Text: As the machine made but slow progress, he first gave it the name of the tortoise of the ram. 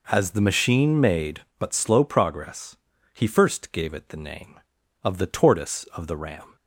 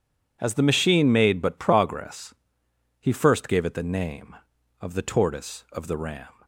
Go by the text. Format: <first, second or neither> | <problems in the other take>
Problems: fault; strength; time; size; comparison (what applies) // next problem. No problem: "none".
first | skips "slow"; at 1.5 s